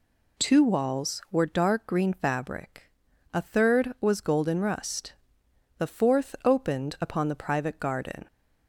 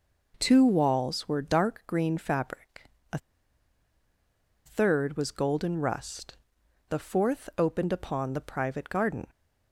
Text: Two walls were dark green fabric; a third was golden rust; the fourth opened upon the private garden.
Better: first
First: none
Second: pauses between "a" and "third"; strong; at 3.1 s; 1.4 s long

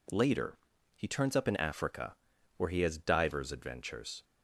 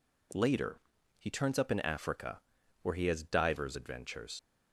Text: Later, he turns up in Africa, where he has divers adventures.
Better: first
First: none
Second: leaves "adventures" unfinished; at 4.3 s; 80 ms

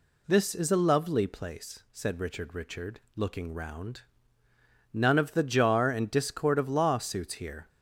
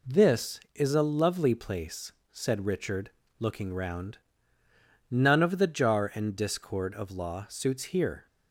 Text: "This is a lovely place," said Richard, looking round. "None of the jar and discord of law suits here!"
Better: second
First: says "Richard" twice; at 2.5 s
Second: none

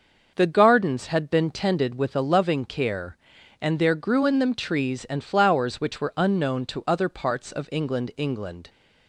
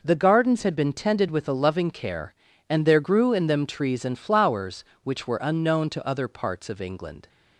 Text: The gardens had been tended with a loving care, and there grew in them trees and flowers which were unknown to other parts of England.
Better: second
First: starts louder than the rest; noticeable; until 1.3 s; 6 dB // says "England" twice; at 8.1 s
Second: none

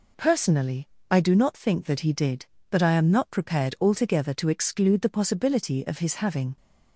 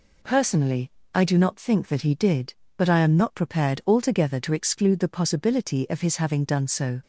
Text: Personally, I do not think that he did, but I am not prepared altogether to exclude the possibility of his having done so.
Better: second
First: stops before "done so"; at 6.5 s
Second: none

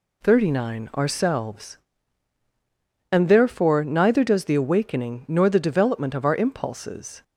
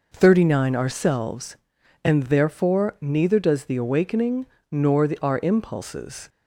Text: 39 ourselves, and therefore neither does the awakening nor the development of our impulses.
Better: first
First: none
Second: pauses between "awakening" and "nor"; slight; at 4.4 s; 0.26 s long // skips "development of"; at 5.1 s

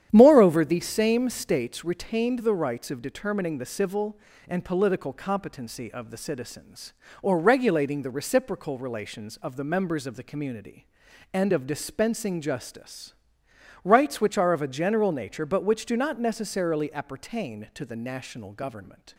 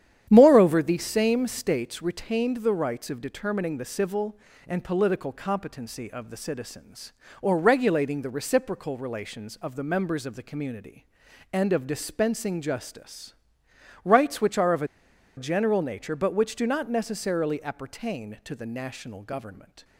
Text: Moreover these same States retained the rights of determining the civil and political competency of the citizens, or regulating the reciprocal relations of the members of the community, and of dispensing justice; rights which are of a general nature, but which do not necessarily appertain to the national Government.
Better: first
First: starts louder than the rest; strong; until 1.1 s; 10 dB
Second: starts louder than the rest; strong; until 1.3 s; 10 dB // pauses between "a" and "general"; noticeable; at 14.8 s; 0.51 s long

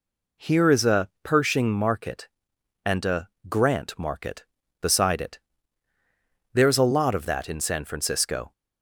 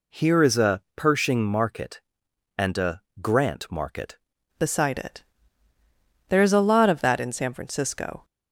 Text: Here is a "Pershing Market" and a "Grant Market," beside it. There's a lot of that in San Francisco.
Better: first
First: pauses between "a" and "Grant"; slight; at 3.2 s; 0.22 s long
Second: pauses between "a" and "Grant"; slight; at 3.0 s; 0.22 s long // changes voice at "beside"; from 4.5 s on; 3.7 s long

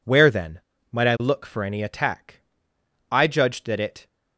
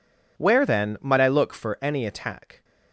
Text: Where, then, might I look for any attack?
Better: second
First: goes on to say "I judged that it"; noticeable; from 3.1 s on; 0.96 s long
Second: none

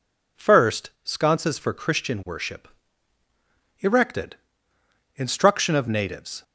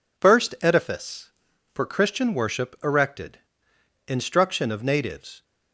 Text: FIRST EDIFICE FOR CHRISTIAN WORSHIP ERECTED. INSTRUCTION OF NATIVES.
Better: second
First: says "Sconces" for "EDIFICE"; at 1.0 s // pauses between "WORSHIP" and "ERECTED"; at 2.6 s; 1.1 s long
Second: none

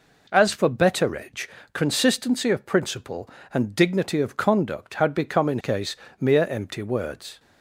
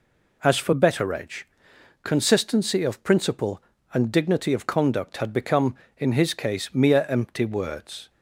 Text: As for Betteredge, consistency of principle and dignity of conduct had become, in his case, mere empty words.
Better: second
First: skips "his"; at 5.5 s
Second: none

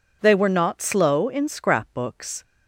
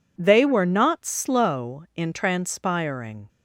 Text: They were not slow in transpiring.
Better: second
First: says "scrapbooks" for "transpiring"; at 1.4 s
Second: none

